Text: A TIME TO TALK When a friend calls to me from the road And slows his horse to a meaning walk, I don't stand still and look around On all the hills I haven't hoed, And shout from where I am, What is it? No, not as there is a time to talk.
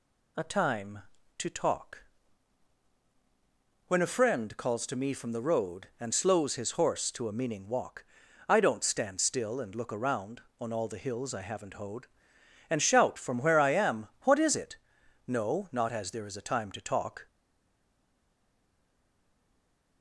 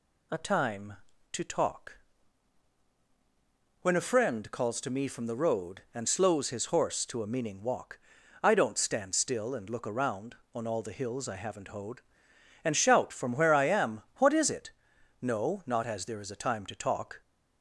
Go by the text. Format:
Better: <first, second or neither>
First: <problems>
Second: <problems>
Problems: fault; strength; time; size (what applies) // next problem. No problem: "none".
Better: second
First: pauses between "TALK" and "When"; strong; at 2.0 s; 1.8 s long // stays silent after the last word; strong; from 17.2 s on; 2.8 s long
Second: pauses between "TALK" and "When"; strong; at 1.9 s; 1.8 s long